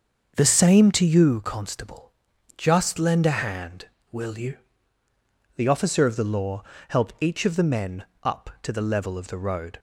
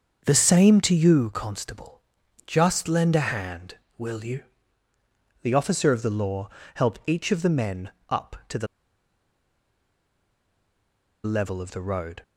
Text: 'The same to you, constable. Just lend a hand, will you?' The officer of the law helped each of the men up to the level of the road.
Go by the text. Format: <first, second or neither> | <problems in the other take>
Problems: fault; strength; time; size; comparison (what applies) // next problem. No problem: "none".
first | starts louder than the rest; until 1.2 s; 7 dB; also in the first // pauses between "law" and "helped"; slight; at 6.4 s; 0.26 s long; slight in the first // pauses between "men" and "up"; slight; at 7.9 s; 0.18 s long; slight in the first // pauses between "the" and "level"; strong; at 8.6 s; 2.5 s long